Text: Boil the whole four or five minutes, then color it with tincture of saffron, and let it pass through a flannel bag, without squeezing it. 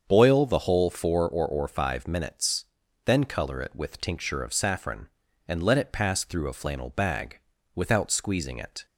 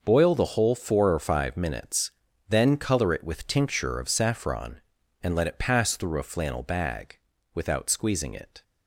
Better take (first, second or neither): second